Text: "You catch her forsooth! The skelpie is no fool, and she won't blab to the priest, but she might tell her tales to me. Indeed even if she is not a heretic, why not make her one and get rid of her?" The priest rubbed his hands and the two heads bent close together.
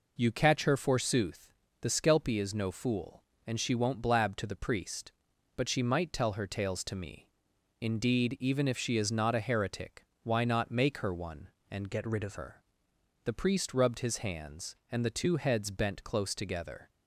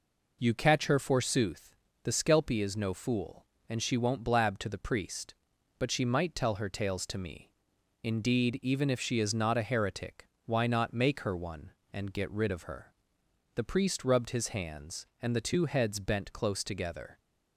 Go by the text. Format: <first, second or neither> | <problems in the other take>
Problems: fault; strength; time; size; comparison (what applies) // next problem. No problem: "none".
second | changes voice from "get" to "of"; from 11.9 to 12.3 s; 0.4 s long